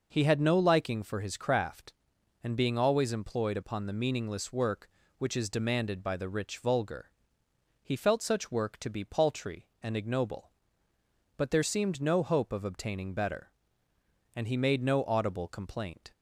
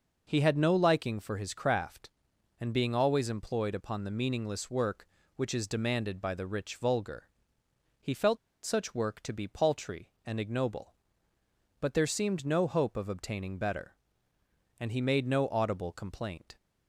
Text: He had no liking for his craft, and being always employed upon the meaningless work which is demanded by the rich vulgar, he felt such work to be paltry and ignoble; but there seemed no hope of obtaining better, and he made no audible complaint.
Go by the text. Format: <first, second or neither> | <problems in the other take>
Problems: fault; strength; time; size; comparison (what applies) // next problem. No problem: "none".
first | pauses between "felt" and "such"; slight; at 8.3 s; 0.25 s long